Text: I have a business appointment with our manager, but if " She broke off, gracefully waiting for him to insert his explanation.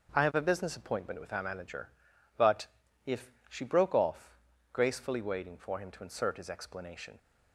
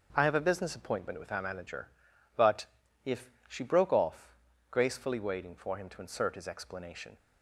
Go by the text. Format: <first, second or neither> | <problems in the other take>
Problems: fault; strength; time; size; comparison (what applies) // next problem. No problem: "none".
neither | starts louder than the rest; the same in both // pauses between "but" and "if"; the same in both